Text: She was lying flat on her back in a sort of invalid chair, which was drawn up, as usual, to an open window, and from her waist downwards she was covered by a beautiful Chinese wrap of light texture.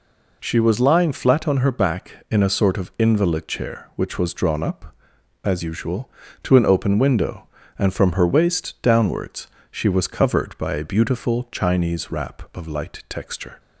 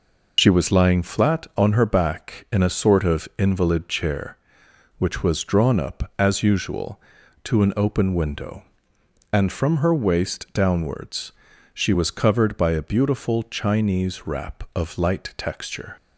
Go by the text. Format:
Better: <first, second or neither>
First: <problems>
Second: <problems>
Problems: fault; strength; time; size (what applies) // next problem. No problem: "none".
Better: first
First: pauses between "downwards" and "she"; slight; at 9.4 s; 0.20 s long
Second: loses the start of "She"; at 0.3 s; 90 ms // pauses between "downwards" and "she"; at 11.3 s; 0.42 s long